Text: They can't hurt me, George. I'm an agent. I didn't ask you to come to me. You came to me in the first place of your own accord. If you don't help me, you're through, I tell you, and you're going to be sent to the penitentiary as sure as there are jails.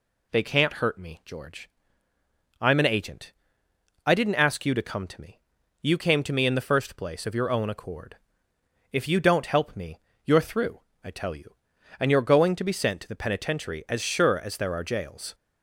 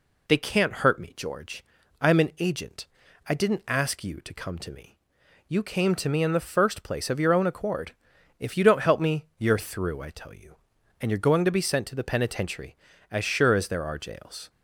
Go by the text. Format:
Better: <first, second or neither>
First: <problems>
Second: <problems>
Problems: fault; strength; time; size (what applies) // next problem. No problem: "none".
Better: neither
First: none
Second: none